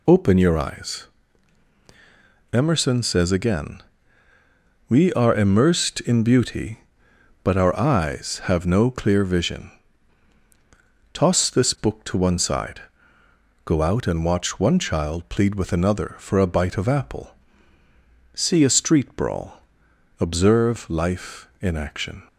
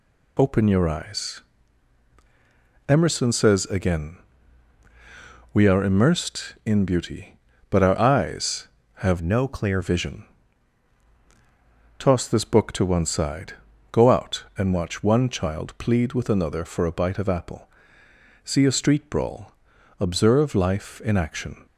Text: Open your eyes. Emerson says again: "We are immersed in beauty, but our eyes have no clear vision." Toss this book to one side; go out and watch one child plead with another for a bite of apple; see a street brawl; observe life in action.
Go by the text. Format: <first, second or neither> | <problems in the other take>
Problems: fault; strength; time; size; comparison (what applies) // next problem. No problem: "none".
first | changes voice from "no" to "clear"; from 9.2 to 9.8 s; 0.6 s long